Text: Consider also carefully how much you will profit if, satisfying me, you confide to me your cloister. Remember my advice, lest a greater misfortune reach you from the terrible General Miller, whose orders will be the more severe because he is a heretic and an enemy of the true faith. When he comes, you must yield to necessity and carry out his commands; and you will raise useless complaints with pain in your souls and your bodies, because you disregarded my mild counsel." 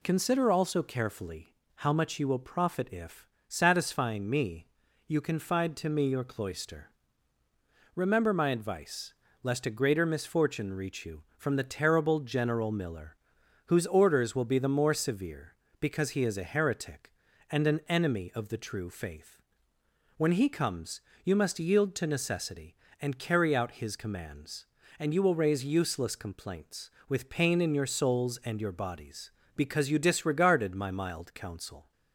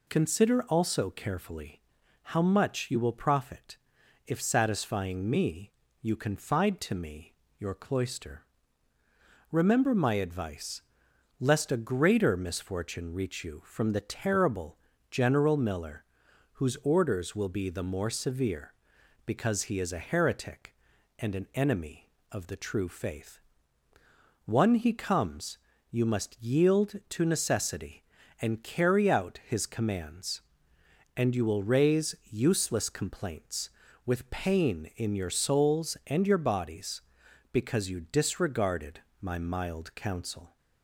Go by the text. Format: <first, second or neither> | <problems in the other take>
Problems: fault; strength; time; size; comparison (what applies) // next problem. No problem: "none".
first | pauses between "carefully" and "how"; at 1.8 s; 0.40 s long; slight in the first // pauses between "profit" and "if"; noticeable; at 3.7 s; 0.50 s long // pauses between "me" and "your"; slight; at 7.3 s; 0.24 s long // pauses between "terrible" and "General"; slight; at 14.7 s; 0.34 s long // says "One" for "When"; at 24.4 s // pauses between "raise" and "useless"; slight; at 32.1 s; 0.16 s long // pauses between "disregarded" and "my"; slight; at 38.9 s; 0.22 s long